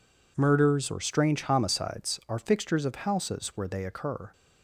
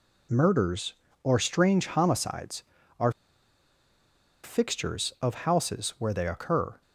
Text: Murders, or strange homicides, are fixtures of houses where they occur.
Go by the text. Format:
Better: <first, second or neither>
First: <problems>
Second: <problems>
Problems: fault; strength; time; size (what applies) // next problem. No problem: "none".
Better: first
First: none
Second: pauses between "are" and "fixtures"; strong; at 3.0 s; 1.3 s long